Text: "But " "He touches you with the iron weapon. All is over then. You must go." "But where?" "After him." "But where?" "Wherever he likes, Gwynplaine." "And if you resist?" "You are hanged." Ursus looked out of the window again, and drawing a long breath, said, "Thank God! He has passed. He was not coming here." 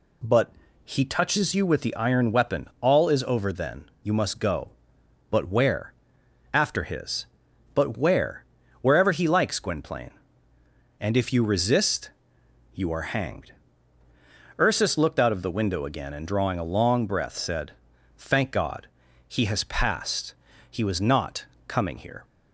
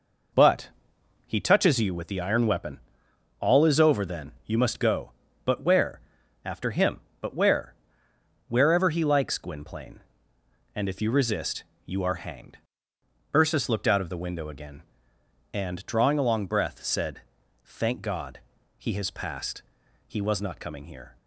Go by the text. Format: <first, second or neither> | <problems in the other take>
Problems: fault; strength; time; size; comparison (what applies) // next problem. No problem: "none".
second | says "his" for "him"; at 6.8 s // pauses between "not" and "coming"; slight; at 21.4 s; 0.20 s long